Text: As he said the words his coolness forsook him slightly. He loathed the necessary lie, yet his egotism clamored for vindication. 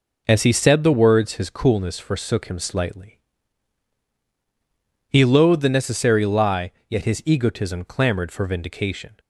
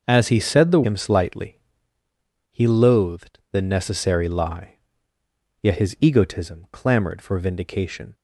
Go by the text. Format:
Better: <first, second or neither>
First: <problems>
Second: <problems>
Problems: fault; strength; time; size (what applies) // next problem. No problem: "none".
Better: first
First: none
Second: skips "words his coolness forsook"; at 0.8 s